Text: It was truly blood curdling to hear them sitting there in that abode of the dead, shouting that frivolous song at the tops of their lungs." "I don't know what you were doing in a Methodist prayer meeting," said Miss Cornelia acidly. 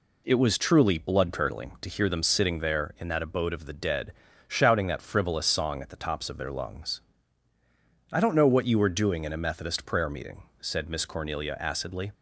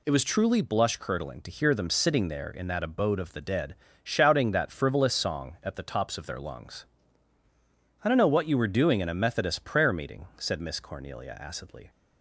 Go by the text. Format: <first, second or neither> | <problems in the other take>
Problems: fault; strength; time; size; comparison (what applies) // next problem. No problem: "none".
first | says "blush" for "blood"; at 0.6 s